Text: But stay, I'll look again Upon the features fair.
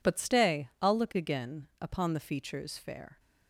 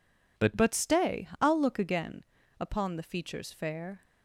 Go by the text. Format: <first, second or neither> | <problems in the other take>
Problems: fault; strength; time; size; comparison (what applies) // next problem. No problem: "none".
first | says "But" twice; at 0.5 s // pauses between "again" and "Upon"; slight; at 2.2 s; 0.36 s long